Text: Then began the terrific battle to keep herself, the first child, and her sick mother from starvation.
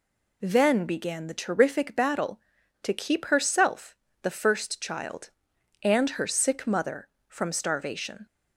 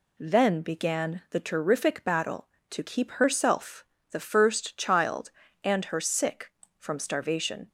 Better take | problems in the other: first | skips "mother"; at 6.6 s

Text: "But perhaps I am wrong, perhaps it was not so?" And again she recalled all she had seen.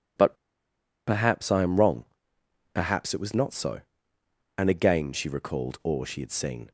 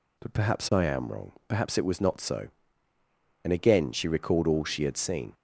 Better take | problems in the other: second | pauses between "But" and "perhaps"; noticeable; at 0.3 s; 0.72 s long

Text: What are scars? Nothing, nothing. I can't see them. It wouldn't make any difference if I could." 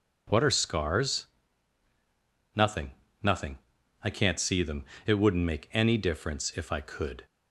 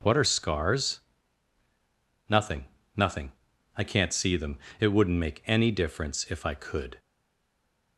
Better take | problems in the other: first | stays silent after the last word; slight; from 6.9 s on; 1.0 s long

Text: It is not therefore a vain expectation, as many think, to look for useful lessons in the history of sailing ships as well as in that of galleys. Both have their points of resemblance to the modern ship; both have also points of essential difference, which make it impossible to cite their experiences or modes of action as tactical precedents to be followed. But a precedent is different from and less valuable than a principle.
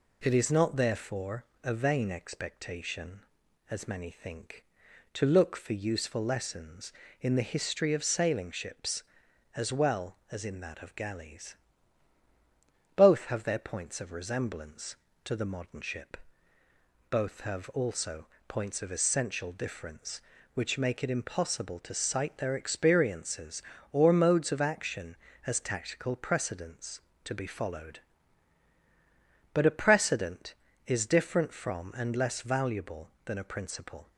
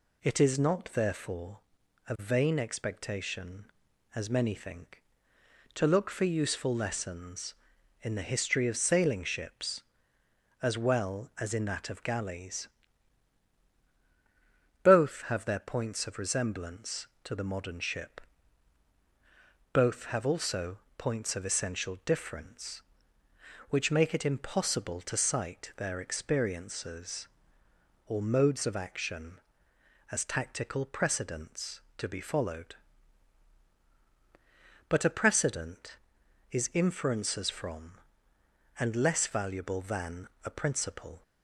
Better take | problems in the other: first | pauses between "therefore" and "a"; noticeable; at 1.5 s; 0.50 s long; slight in the first // pauses between "also" and "points"; slight; at 20.7 s; 0.20 s long; slight in the first // says "inferences" for "different"; at 36.7 s // pauses between "than" and "a"; slight; at 40.2 s; 0.16 s long

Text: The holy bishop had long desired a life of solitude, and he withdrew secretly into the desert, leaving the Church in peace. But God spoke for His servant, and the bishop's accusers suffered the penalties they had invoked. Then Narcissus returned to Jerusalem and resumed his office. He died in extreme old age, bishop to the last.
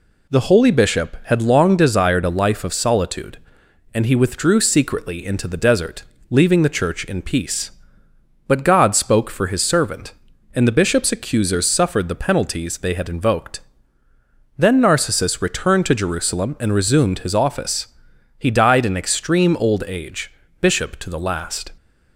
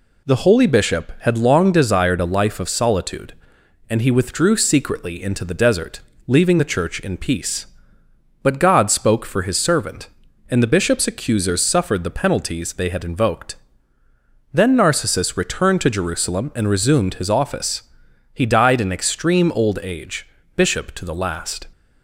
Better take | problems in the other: neither | none

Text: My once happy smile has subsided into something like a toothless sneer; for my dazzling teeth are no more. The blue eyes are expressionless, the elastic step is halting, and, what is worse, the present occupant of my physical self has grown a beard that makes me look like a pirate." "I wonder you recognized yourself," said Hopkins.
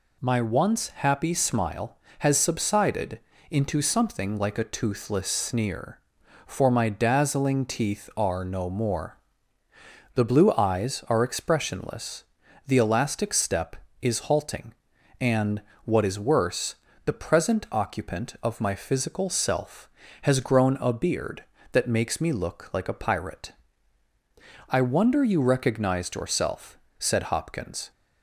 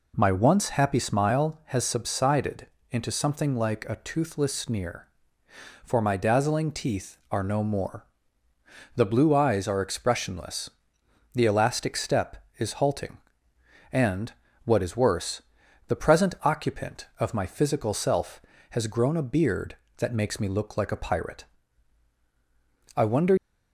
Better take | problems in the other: first | pauses between "subsided" and "into"; slight; at 2.6 s; 0.26 s long; slight in the first // stops before "you recognized yourself said Hopkins"; at 23.3 s

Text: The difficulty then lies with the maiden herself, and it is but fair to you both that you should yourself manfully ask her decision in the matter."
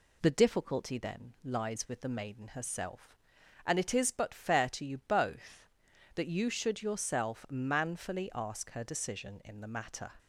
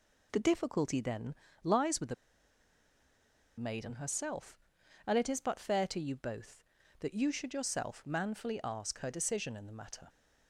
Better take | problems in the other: first | pauses between "then" and "lies"; slight; at 1.3 s; 0.28 s long // pauses between "the" and "maiden"; strong; at 2.1 s; 1.4 s long

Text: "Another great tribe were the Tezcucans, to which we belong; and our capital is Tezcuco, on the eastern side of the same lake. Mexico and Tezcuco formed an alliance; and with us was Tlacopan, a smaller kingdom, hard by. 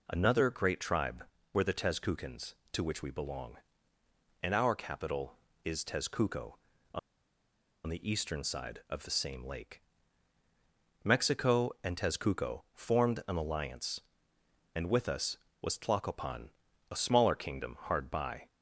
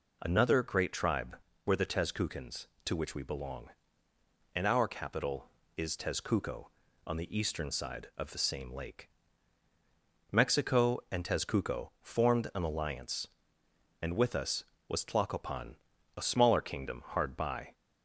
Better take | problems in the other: second | pauses between "on" and "the"; noticeable; at 6.9 s; 0.87 s long

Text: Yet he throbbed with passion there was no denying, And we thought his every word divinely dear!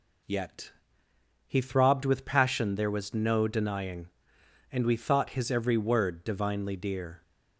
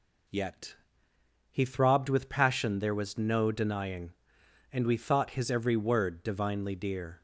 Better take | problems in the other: neither | pauses between "Yet" and "he"; noticeable; the same in both

